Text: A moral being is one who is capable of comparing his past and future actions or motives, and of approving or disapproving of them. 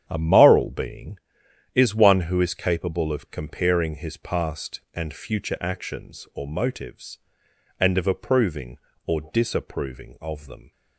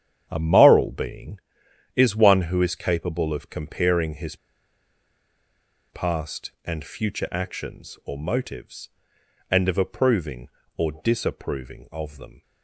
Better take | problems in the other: first | starts louder than the rest; strong; until 1.3 s; 9 dB; strong in the first // pauses between "his" and "past"; strong; at 4.3 s; 1.5 s long

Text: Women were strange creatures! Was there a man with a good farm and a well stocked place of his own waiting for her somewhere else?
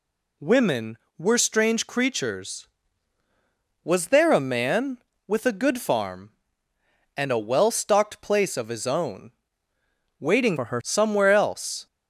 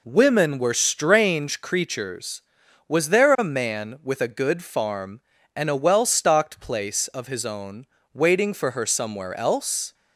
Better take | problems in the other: second | pauses between "own" and "waiting"; noticeable; at 9.3 s; 0.88 s long; slight in the second // changes voice from "for" to "her"; from 10.5 to 10.8 s; 0.3 s long

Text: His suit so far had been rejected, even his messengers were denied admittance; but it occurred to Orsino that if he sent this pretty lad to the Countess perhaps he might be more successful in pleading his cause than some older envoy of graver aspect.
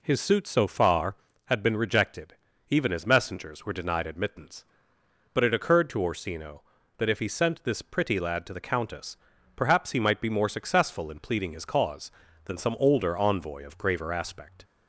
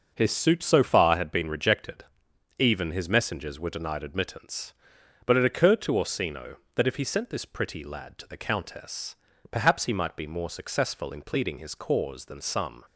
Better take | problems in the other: first | pauses between "Countess" and "perhaps"; slight; at 9.1 s; 0.34 s long; also in the first // stops before "older envoy of graver aspect"; at 12.8 s

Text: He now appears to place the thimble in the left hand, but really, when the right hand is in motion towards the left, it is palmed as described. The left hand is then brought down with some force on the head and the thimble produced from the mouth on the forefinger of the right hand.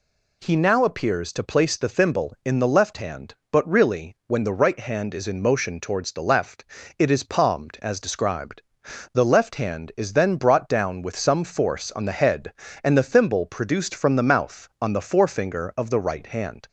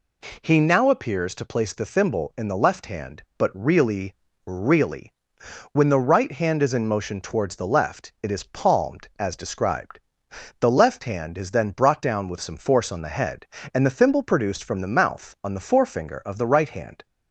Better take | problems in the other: first | says "really" twice; at 4.4 s

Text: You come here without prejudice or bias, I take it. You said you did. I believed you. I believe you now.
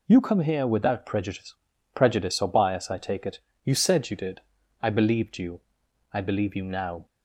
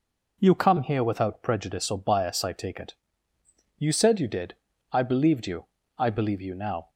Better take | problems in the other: second | says "prejudice" twice; at 1.9 s

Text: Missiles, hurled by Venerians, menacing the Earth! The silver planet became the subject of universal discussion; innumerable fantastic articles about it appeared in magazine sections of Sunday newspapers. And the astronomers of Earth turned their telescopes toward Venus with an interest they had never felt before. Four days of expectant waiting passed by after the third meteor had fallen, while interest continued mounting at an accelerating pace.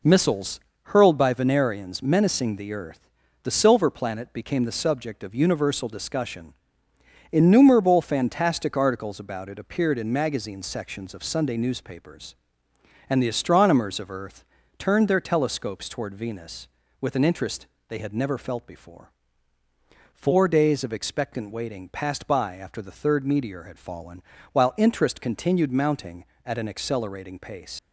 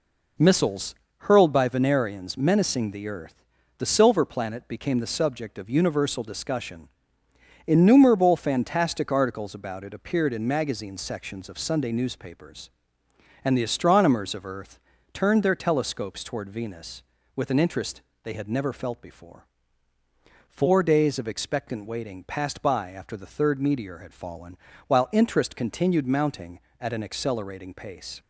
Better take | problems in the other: second | pauses between "Earth" and "turned"; slight; at 14.4 s; 0.36 s long; slight in the second // pauses between "interest" and "they"; slight; at 17.6 s; 0.20 s long; slight in the second // leaves "pace" unfinished; at 27.7 s; 65 ms

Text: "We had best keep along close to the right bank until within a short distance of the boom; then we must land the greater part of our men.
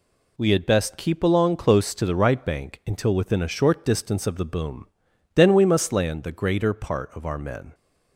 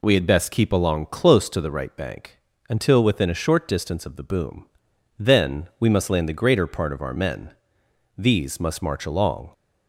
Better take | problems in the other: first | pauses between "bank" and "until"; slight; at 2.3 s; 0.30 s long // goes on to say "These must march along"; from 8.1 s on; 1.3 s long

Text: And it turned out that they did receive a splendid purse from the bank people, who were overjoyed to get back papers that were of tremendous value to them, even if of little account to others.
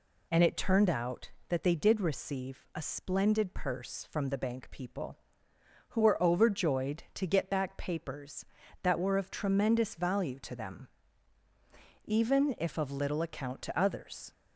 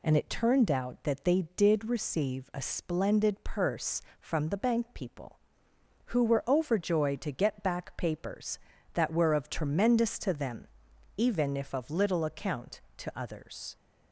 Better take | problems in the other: first | skips "value"; at 10.1 s

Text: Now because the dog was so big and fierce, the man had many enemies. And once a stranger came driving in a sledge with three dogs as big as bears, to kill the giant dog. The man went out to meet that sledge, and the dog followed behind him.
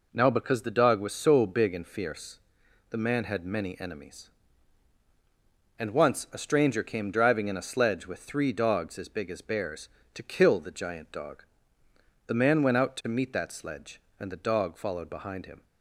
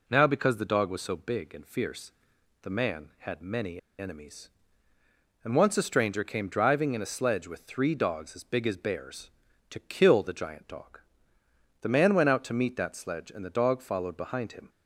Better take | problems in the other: first | pauses between "many" and "enemies"; slight; at 3.7 s; 0.20 s long

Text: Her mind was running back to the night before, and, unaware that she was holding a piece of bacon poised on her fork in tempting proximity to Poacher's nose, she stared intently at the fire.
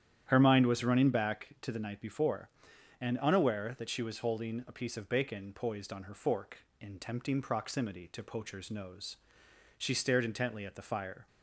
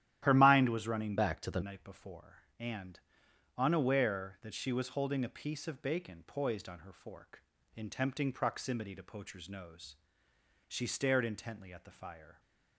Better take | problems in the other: first | starts louder than the rest; strong; until 1.2 s; 12 dB; strong in the first // changes voice from "back" to "the"; from 1.1 to 1.6 s; 0.5 s long

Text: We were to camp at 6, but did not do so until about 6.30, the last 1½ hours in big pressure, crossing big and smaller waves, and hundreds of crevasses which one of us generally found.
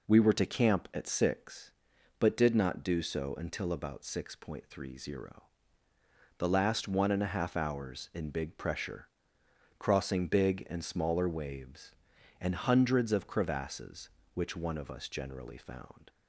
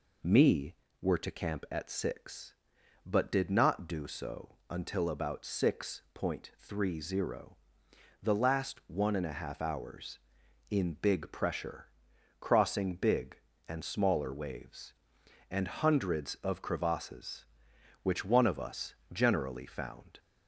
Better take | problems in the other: first | says "Me" for "We"; at 0.2 s // pauses between "us" and "generally"; slight; at 18.9 s; 0.18 s long

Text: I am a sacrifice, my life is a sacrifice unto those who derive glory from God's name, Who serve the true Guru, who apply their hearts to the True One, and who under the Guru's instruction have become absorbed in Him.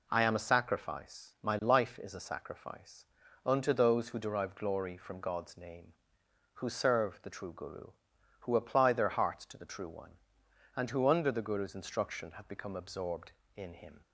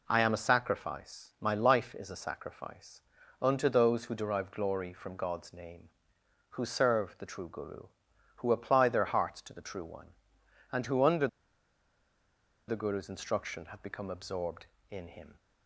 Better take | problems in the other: first | pauses between "sacrifice" and "unto"; at 3.0 s; 0.40 s long; also in the first // pauses between "under" and "the"; strong; at 11.2 s; 1.4 s long

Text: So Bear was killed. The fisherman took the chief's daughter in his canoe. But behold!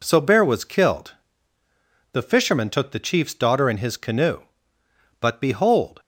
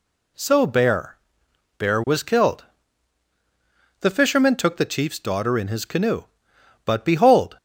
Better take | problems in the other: first | says "Bear" twice; at 1.7 s

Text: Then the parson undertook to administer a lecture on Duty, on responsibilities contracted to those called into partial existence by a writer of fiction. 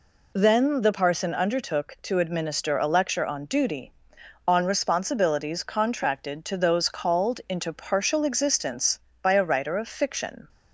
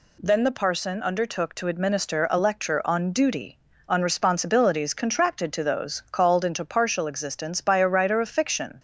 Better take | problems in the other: neither | none

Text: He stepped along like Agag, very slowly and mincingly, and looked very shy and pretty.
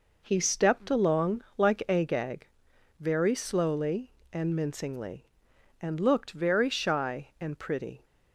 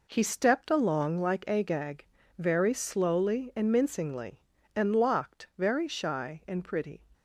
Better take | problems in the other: first | says "locked" for "looked"; at 4.9 s

